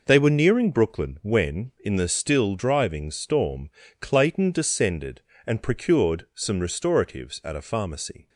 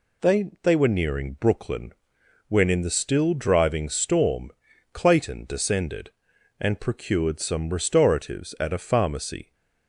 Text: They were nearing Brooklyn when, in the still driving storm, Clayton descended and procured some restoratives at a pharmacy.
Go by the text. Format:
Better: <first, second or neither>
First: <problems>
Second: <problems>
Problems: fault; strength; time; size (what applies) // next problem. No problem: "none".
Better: first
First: none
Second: says "They" twice; at 0.6 s // pauses between "Brooklyn" and "when"; noticeable; at 1.9 s; 0.56 s long